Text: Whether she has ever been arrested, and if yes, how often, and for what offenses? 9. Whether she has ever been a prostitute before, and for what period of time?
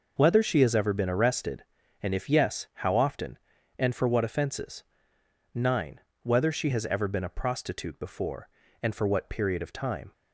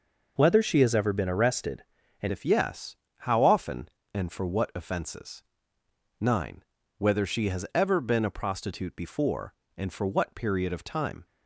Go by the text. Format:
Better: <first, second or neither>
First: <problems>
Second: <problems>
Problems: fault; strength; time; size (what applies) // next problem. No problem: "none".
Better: first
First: none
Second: changes voice at "if"; from 2.3 s on; 8.9 s long